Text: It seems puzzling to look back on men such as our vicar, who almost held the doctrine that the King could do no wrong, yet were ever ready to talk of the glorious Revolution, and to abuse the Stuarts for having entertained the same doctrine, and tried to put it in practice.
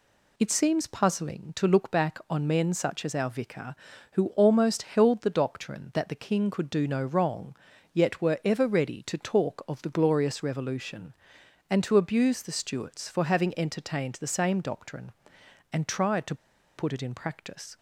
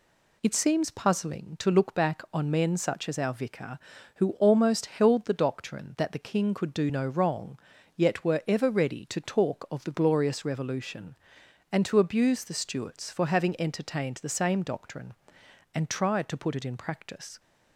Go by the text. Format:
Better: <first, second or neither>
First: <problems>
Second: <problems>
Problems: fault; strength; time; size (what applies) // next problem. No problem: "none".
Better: second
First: pauses between "to" and "put"; at 16.3 s; 0.41 s long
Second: none